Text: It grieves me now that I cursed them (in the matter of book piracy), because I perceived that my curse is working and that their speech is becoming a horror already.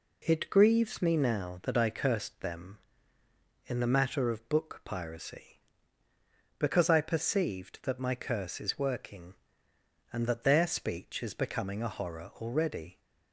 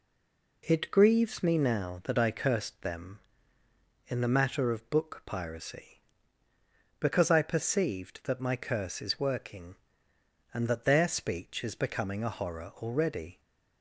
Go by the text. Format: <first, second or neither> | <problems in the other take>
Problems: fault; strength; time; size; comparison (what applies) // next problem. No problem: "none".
first | stays silent before the first word; slight; until 0.6 s; 0.6 s long